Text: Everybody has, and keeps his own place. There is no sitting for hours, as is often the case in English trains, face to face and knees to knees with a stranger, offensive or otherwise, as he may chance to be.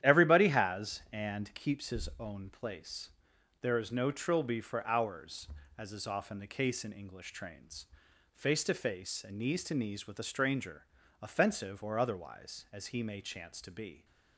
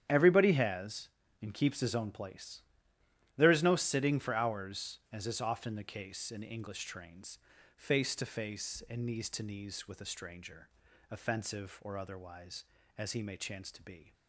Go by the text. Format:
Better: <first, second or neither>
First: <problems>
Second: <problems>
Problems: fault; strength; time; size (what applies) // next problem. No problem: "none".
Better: second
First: starts louder than the rest; strong; until 1.0 s; 11 dB // says "trilby" for "sitting"; at 4.1 s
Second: starts louder than the rest; strong; until 1.0 s; 9.5 dB